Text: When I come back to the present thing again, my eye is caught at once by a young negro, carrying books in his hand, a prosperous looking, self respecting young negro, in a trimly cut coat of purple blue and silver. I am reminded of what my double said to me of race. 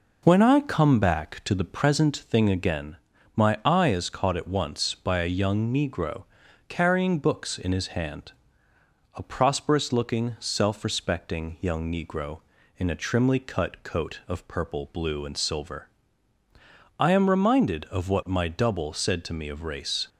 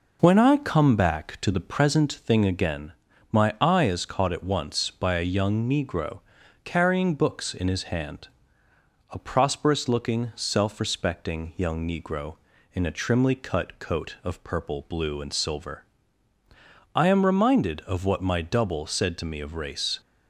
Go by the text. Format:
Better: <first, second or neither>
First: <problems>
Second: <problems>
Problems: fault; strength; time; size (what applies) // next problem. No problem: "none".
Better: neither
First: none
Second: none